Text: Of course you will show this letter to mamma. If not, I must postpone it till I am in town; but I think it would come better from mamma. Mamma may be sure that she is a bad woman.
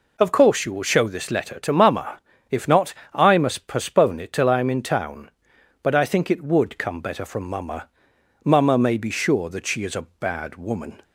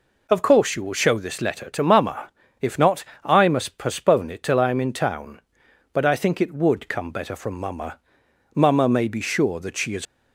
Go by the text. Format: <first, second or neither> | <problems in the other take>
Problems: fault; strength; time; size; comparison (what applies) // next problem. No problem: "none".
first | stops before "a bad woman"; at 10.0 s